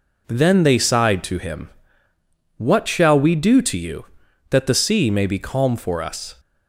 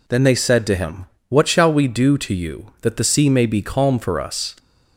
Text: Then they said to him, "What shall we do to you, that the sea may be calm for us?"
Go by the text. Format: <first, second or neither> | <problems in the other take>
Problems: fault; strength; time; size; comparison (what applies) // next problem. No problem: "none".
second | says "sighed" for "said"; at 0.7 s